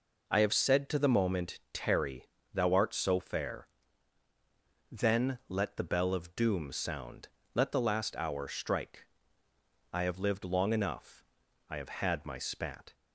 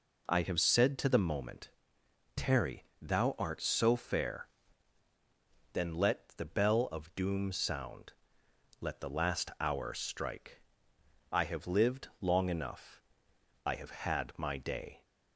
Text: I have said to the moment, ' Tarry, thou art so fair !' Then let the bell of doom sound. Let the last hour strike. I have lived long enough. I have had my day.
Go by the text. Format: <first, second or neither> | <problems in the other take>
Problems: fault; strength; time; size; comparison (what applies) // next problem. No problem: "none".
second | says "spat" for "day"; at 12.3 s